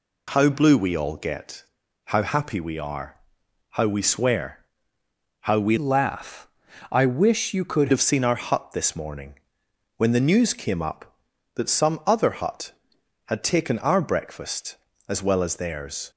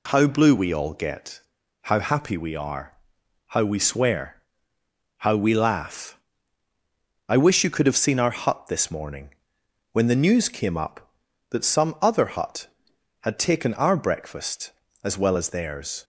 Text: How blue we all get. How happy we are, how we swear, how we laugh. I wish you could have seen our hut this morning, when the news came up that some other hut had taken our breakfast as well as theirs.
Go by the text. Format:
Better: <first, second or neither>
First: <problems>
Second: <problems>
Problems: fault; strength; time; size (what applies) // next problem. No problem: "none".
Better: second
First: changes voice from "laugh" to "could"; from 5.7 to 7.8 s; 2.1 s long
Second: none